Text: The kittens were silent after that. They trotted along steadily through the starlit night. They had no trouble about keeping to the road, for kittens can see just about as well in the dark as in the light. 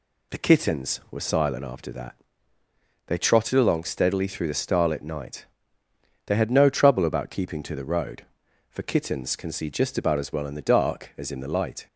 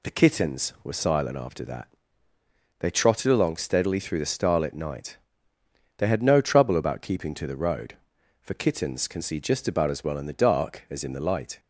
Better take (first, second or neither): neither